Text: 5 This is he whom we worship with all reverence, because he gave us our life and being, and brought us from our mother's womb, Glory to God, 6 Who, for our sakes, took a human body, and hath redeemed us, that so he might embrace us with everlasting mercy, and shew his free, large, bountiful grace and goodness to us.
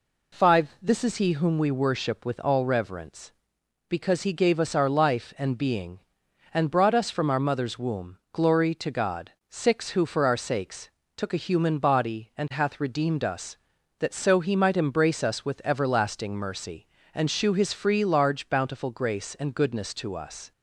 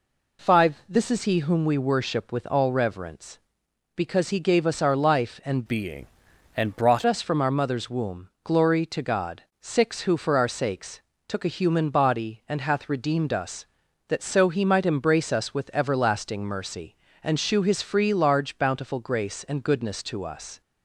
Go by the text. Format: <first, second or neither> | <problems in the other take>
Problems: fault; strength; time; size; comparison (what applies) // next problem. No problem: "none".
first | changes voice from "being" to "brought"; from 5.6 to 7.0 s; 1.4 s long